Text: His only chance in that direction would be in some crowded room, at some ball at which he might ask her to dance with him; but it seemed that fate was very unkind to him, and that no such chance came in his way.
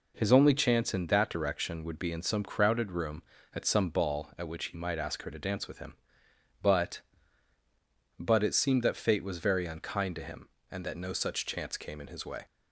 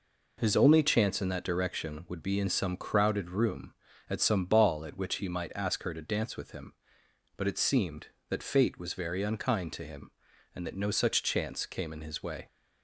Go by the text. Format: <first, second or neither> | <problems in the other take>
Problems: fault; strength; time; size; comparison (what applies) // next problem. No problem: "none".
second | says "but" twice; at 8.1 s